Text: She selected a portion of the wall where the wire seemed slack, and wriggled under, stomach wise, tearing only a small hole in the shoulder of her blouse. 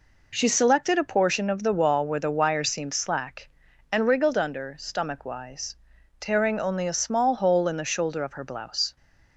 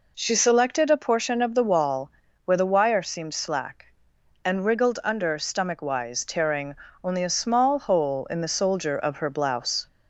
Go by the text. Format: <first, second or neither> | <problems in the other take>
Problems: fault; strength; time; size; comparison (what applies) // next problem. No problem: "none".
first | pauses between "wall" and "where"; slight; at 2.0 s; 0.36 s long // pauses between "tearing" and "only"; slight; at 6.7 s; 0.30 s long // says "soldier" for "shoulder"; at 8.4 s